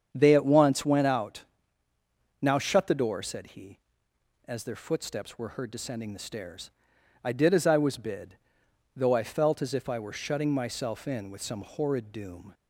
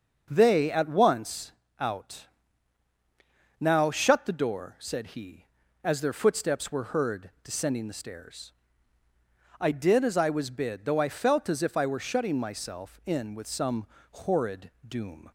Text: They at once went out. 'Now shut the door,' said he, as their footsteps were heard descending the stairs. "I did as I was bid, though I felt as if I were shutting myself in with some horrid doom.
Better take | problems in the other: first | starts louder than the rest; until 1.3 s; 6.5 dB; strong in the first // skips "went"; at 1.6 s // pauses between "some" and "horrid"; slight; at 13.8 s; 0.24 s long // pauses between "horrid" and "doom"; slight; at 14.7 s; 0.16 s long

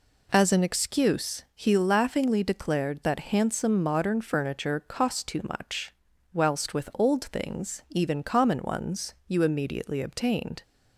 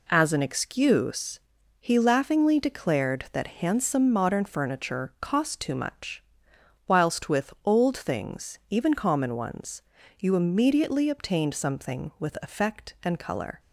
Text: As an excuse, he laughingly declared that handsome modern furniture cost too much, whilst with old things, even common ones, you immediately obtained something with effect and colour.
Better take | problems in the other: second | stops before "something with effect and colour"; at 10.6 s

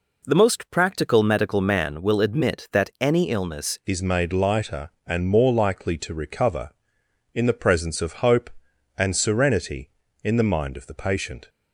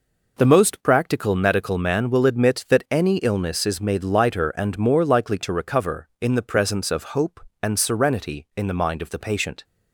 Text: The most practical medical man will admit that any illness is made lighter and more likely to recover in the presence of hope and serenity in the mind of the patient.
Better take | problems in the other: second | changes voice at "is"; from 3.8 s on; 7.6 s long

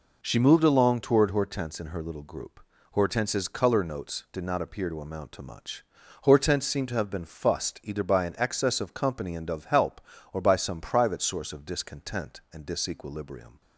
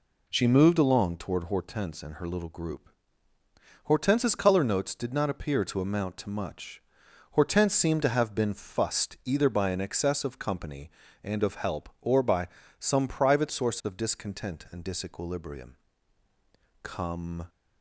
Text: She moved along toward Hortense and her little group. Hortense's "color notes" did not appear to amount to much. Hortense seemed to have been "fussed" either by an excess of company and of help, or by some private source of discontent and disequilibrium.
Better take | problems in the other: first | pauses between "by" and "some"; slight; at 12.4 s; 0.32 s long // goes on to say "Come"; noticeable; from 16.8 s on; 0.66 s long

